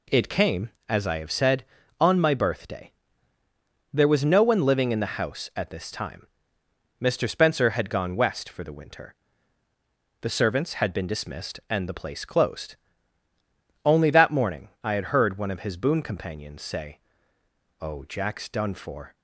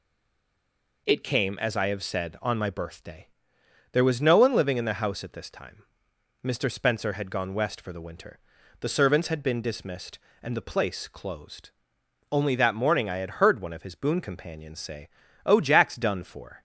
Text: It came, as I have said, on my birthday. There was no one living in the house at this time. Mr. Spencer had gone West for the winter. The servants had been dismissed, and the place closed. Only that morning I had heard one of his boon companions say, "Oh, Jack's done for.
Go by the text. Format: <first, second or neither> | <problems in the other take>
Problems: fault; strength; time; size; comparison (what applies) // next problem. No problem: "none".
first | stays silent before the first word; until 1.0 s; 1.0 s long